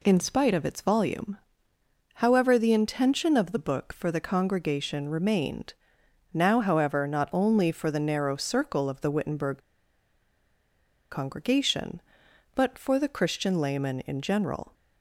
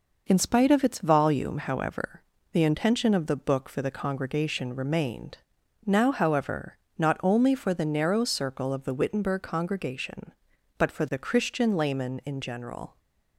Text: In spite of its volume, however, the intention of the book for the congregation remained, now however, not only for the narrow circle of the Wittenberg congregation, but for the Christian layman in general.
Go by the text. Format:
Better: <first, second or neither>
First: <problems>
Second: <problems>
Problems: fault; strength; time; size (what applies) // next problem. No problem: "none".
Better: second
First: pauses between "Wittenberg" and "congregation"; strong; at 9.5 s; 1.5 s long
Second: none